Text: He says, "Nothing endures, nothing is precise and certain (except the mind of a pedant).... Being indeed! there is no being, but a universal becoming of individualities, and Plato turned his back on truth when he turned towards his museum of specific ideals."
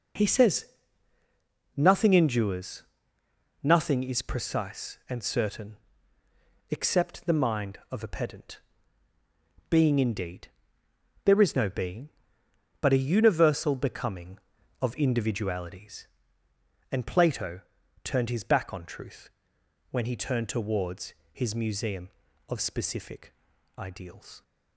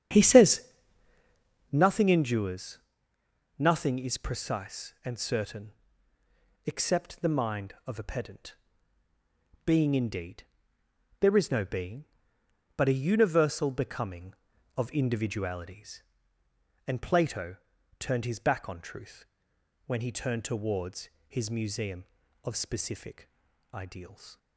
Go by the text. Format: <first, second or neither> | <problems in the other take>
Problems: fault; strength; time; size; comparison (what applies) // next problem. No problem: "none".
first | starts louder than the rest; strong; until 1.8 s; 8.5 dB // pauses between "Plato" and "turned"; at 17.5 s; 0.42 s long; also in the first // pauses between "truth" and "when"; noticeable; at 19.2 s; 0.62 s long; noticeable in the first // pauses between "towards" and "his"; slight; at 21.0 s; 0.22 s long; slight in the first // pauses between "specific" and "ideals"; at 23.2 s; 0.42 s long; also in the first